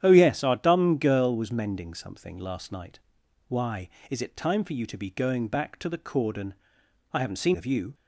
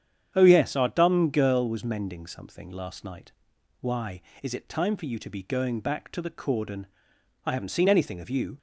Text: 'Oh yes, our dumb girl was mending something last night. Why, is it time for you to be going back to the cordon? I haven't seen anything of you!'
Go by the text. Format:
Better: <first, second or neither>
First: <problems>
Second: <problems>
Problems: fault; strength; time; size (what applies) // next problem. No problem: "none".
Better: second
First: starts louder than the rest; strong; until 1.0 s; 10 dB // skips "anything"; at 7.5 s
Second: starts louder than the rest; strong; until 1.3 s; 8.5 dB